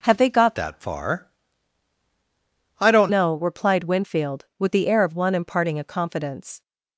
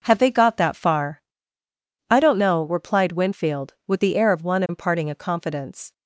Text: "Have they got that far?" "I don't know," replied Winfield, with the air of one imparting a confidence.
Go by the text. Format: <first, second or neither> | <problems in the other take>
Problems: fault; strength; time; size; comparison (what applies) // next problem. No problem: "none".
second | changes voice from "that" to "don't"; from 0.5 to 3.0 s; 2.5 s long